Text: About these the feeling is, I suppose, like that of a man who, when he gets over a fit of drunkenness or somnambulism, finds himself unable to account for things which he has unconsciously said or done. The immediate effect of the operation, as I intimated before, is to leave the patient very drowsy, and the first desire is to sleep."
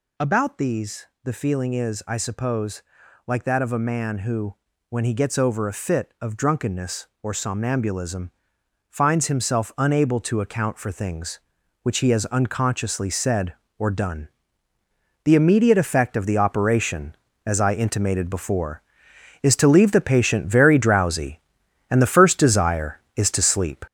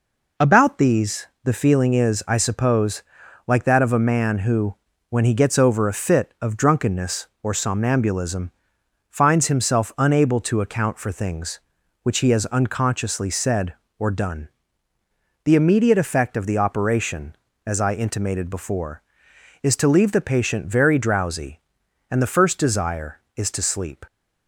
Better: second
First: gets louder; throughout; 6.5 dB // pauses between "these" and "the"; slight; at 1.0 s; 0.18 s long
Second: pauses between "these" and "the"; slight; at 1.2 s; 0.18 s long

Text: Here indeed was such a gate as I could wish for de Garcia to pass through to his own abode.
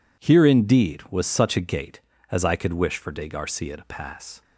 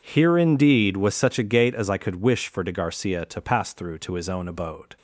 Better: second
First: stops before "through to his own abode"; at 4.4 s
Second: none

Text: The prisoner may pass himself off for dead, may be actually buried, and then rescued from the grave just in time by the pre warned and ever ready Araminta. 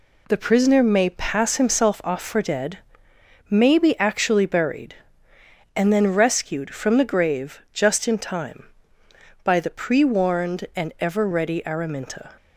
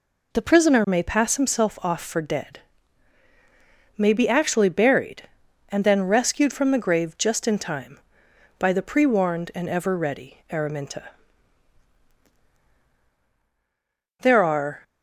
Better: first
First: none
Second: goes on to say "There are"; noticeable; from 14.2 s on; 0.62 s long

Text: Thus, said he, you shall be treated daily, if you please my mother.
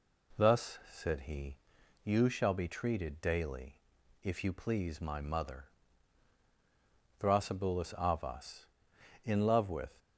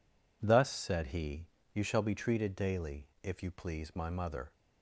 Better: second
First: goes on to say "Thrasybulus Avas in love with"; strong; from 7.1 s on; 2.7 s long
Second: none

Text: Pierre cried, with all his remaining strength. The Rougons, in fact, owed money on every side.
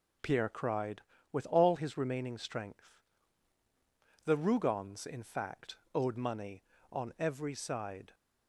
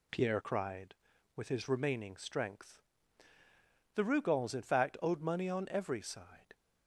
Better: first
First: none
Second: skips "all"; at 1.4 s

